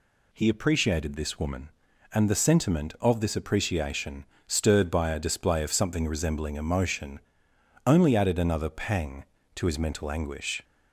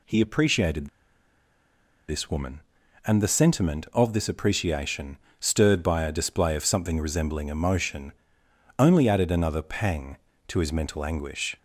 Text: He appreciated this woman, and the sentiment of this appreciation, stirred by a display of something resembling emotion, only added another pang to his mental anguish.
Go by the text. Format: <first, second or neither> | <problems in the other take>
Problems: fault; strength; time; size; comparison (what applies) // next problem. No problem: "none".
first | pauses between "appreciated" and "this"; at 0.8 s; 1.2 s long